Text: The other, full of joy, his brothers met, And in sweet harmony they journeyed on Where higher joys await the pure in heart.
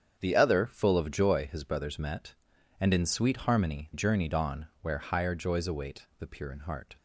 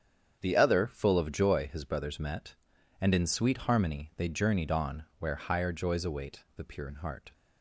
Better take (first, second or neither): second